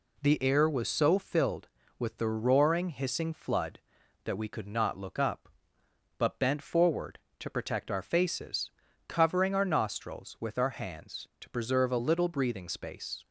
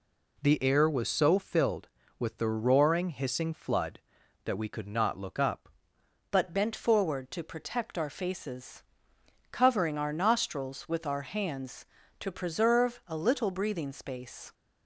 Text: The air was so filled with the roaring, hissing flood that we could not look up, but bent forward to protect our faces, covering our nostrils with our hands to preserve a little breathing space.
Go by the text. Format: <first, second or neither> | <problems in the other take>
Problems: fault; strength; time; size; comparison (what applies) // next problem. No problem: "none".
first | changes voice at "but"; from 6.3 s on; 8.2 s long